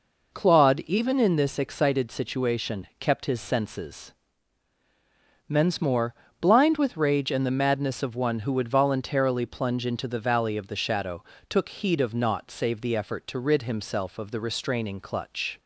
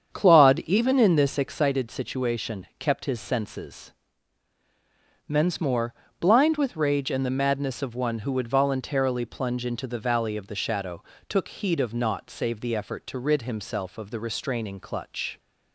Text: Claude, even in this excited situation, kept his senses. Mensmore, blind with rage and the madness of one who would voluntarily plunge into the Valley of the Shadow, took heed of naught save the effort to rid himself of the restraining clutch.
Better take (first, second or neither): first